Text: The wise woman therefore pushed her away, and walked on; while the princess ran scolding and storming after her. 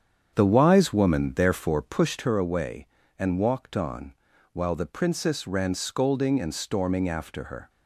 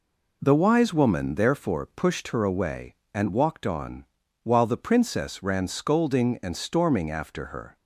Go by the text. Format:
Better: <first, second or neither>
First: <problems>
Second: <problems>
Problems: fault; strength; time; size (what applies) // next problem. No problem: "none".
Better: second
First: starts louder than the rest; strong; until 2.3 s; 8 dB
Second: none